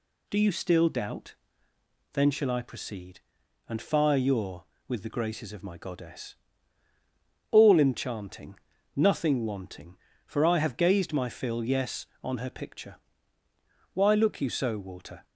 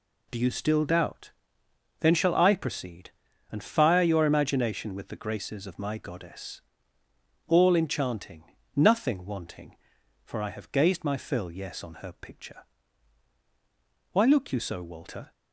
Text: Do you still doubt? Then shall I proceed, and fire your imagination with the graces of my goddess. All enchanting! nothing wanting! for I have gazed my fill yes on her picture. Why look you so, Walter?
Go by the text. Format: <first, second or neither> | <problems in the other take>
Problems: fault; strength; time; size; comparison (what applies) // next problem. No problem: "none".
second | skips "imagination"; at 4.7 s